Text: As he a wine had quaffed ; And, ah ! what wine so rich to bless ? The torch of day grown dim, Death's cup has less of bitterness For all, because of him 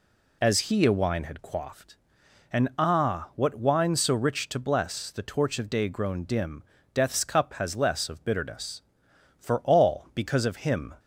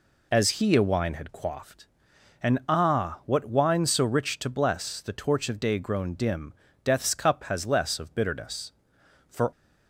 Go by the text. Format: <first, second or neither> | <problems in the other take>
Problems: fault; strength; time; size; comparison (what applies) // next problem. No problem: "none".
first | stops before "all because of him"; at 9.5 s